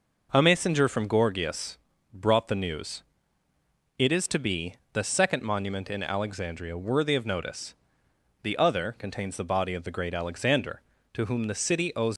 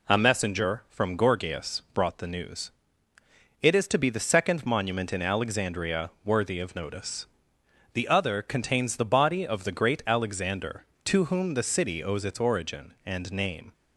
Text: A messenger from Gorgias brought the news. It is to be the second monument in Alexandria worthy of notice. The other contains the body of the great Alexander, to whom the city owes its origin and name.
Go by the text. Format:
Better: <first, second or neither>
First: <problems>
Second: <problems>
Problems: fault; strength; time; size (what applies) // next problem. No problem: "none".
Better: second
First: pauses between "Gorgias" and "brought"; at 1.7 s; 0.38 s long // pauses between "be" and "the"; slight; at 4.7 s; 0.16 s long // stops before "its origin and name"; at 12.1 s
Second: none